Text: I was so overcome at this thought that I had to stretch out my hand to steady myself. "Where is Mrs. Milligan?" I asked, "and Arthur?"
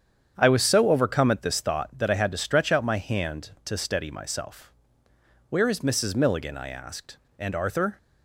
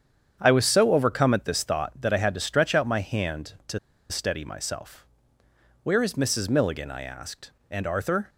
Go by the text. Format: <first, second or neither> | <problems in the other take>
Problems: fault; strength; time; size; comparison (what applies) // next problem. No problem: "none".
first | starts louder than the rest; strong; until 1.4 s; 8 dB; strong in the first // pauses between "to" and "steady"; slight; at 3.7 s; 0.32 s long